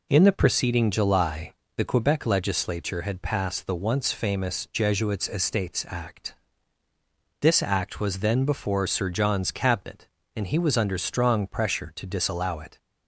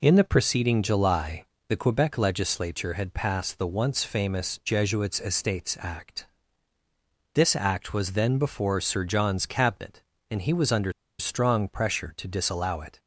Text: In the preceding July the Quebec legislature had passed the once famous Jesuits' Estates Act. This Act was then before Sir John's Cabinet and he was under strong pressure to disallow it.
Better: first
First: pauses between "July" and "the"; slight; at 1.5 s; 0.24 s long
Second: pauses between "July" and "the"; slight; at 1.4 s; 0.24 s long // pauses between "under" and "strong"; slight; at 10.9 s; 0.28 s long

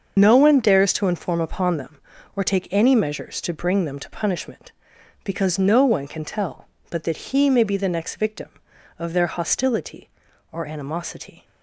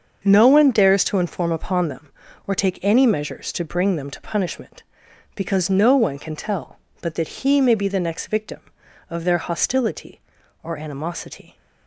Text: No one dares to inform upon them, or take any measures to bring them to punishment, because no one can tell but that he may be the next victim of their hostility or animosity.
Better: second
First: loses the start of "No"; at 0.1 s; 45 ms // starts louder than the rest; until 1.1 s; 6.5 dB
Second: starts louder than the rest; until 1.2 s; 6.5 dB

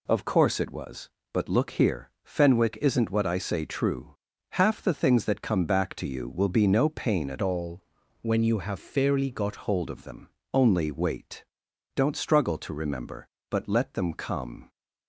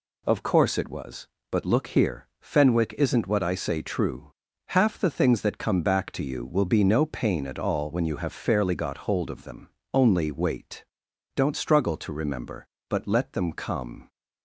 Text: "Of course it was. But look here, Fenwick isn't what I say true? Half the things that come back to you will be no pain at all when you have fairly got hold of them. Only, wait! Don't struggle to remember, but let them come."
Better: second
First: changes voice from "all" to "got"; from 7.4 to 9.5 s; 2.1 s long // pauses between "all" and "when"; at 7.8 s; 0.42 s long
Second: none

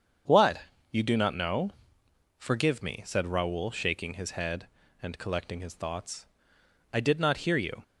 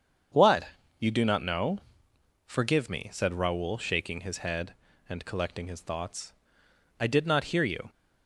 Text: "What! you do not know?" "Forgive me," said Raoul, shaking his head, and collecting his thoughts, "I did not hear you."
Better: neither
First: starts louder than the rest; strong; until 1.6 s; 7 dB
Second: starts louder than the rest; strong; until 1.6 s; 7 dB

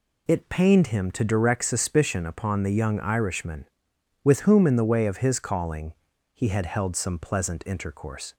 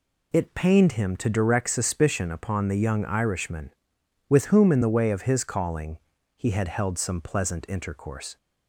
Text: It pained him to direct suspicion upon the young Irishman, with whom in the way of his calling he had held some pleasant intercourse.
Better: neither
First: pauses between "calling" and "he"; at 5.9 s; 0.42 s long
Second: pauses between "calling" and "he"; at 5.9 s; 0.40 s long

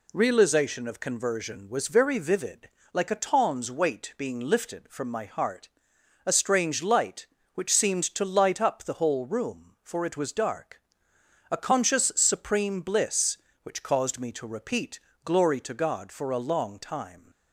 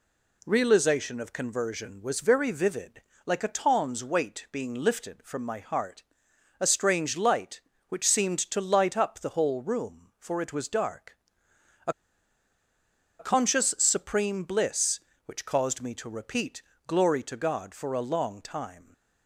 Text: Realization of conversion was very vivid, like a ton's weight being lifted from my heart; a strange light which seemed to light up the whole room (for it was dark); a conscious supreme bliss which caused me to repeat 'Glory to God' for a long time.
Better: first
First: pauses between "repeat" and "Glory"; slight; at 14.9 s; 0.24 s long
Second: pauses between "a" and "conscious"; strong; at 11.9 s; 1.2 s long // pauses between "repeat" and "Glory"; slight; at 16.6 s; 0.24 s long

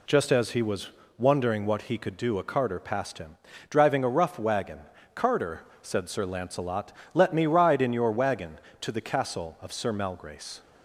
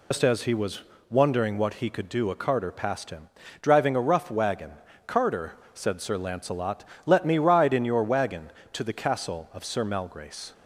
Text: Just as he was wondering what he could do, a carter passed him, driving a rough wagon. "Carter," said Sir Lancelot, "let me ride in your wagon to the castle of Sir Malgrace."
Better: first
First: pauses between "was" and "wondering"; slight; at 0.8 s; 0.30 s long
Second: loses the start of "Just"; at 0.1 s; 120 ms // pauses between "was" and "wondering"; slight; at 0.8 s; 0.30 s long

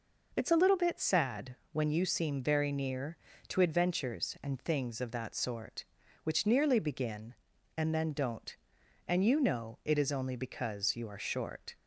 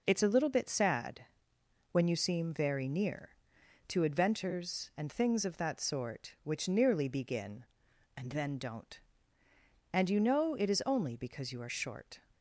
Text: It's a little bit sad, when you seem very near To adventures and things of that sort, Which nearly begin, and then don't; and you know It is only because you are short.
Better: neither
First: none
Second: none

